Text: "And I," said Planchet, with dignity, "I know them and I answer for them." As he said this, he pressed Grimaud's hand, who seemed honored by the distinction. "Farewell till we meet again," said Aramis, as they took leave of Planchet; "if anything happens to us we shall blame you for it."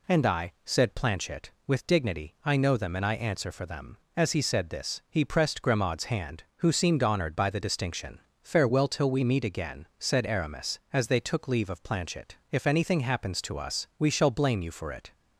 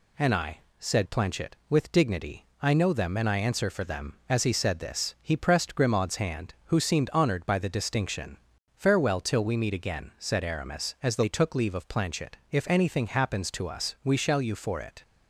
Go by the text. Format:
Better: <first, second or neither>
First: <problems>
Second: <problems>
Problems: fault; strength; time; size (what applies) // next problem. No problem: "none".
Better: first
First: none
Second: skips "blame"; at 14.4 s